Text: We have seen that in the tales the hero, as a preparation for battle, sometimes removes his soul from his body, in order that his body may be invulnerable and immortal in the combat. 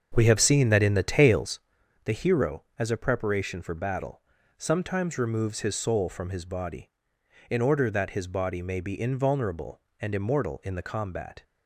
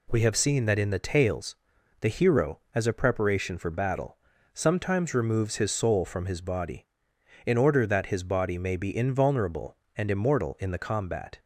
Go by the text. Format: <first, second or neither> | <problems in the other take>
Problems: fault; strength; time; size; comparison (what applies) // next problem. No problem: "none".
second | starts louder than the rest; until 1.8 s; 6.5 dB // pauses between "tales" and "the"; noticeable; at 1.5 s; 0.46 s long; noticeable in the second